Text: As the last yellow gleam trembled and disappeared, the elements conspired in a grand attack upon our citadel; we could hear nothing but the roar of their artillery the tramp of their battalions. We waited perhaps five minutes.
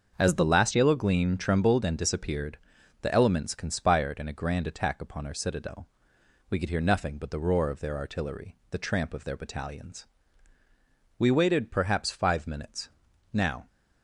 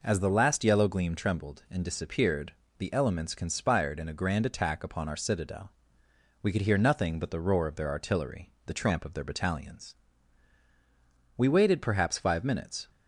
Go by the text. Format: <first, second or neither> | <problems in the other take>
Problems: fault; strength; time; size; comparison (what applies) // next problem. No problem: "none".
second | starts louder than the rest; until 1.1 s; 6.5 dB // pauses between "artillery" and "the"; slight; at 8.5 s; 0.16 s long // goes on to say "Now"; slight; from 13.3 s on; 0.34 s long